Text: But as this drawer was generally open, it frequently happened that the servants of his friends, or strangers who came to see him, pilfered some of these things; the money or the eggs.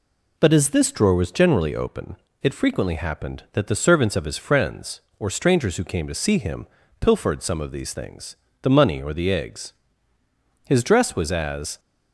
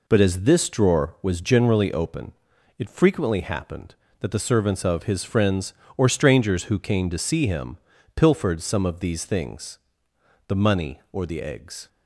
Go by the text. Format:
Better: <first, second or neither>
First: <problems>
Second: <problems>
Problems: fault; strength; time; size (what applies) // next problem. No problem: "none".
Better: second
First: goes on to say "His dress was as"; noticeable; from 10.6 s on; 1.1 s long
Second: none